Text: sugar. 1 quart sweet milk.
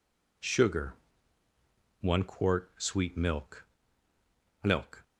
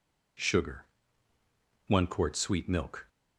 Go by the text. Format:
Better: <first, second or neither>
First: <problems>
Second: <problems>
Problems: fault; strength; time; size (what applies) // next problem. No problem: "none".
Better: second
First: says "milk" twice; at 4.6 s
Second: none